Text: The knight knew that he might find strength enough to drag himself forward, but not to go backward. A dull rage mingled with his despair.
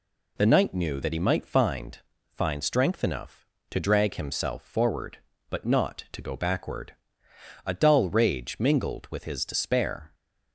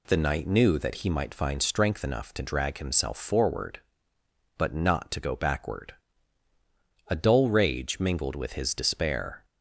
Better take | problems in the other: second | says "find" twice; at 2.2 s

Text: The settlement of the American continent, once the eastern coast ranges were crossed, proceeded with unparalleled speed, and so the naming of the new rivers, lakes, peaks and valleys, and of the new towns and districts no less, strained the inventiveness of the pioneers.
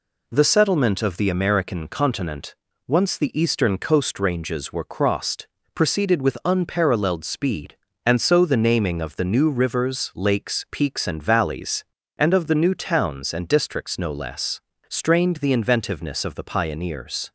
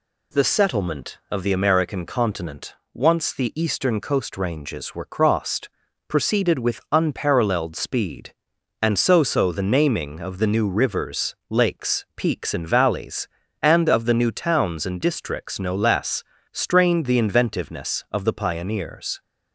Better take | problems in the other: first | says "so" twice; at 9.2 s

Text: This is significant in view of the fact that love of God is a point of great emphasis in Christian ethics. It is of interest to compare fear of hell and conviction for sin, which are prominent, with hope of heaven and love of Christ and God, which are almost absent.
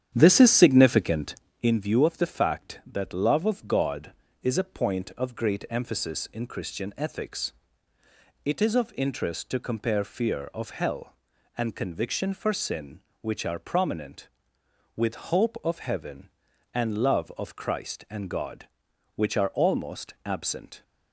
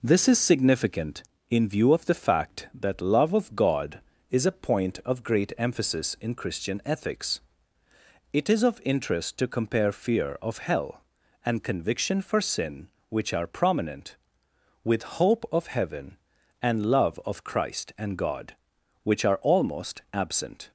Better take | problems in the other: second | starts louder than the rest; strong; until 1.8 s; 9.5 dB

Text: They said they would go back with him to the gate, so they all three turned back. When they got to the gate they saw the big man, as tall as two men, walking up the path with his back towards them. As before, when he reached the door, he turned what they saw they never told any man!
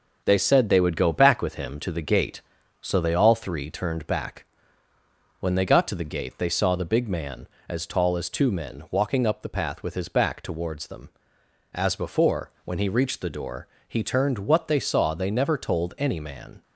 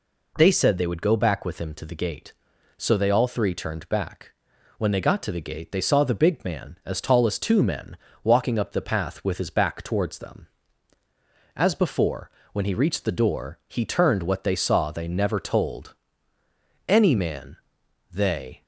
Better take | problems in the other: first | pauses between "told" and "any"; noticeable; at 15.9 s; 0.92 s long // goes on to say "They"; from 18.1 s on; 0.50 s long

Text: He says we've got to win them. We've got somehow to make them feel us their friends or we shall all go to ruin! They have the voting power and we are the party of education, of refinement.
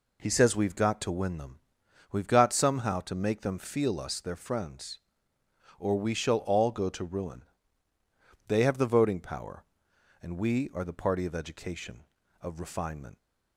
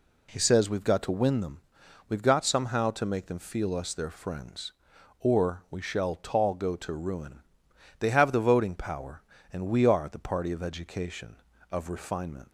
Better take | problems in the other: first | says "tall" for "all"; at 6.1 s

